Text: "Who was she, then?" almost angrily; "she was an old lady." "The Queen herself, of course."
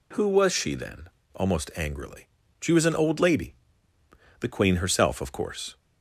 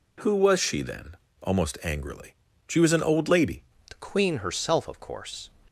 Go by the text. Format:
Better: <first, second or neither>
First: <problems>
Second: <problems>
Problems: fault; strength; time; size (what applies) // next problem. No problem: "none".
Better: first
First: none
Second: changes voice at "The"; from 3.8 s on; 1.6 s long